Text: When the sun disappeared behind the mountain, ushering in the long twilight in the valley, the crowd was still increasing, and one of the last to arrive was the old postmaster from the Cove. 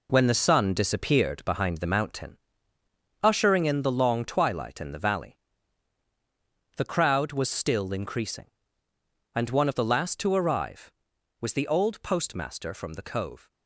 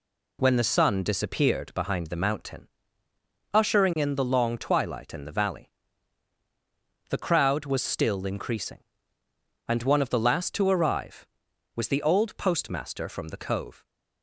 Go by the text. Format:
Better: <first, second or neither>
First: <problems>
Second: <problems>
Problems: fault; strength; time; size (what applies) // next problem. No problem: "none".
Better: second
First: gets quieter; strong; throughout; 8.5 dB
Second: none